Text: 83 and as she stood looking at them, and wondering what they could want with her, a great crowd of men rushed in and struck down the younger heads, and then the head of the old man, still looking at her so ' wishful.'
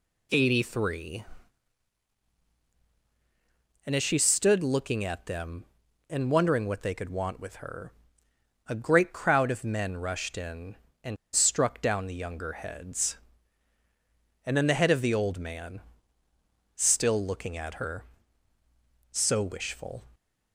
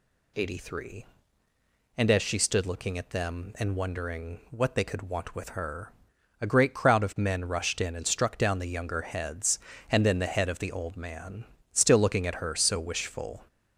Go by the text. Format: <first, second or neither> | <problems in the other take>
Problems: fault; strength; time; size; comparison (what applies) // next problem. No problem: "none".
second | pauses between "and" and "struck"; slight; at 11.1 s; 0.18 s long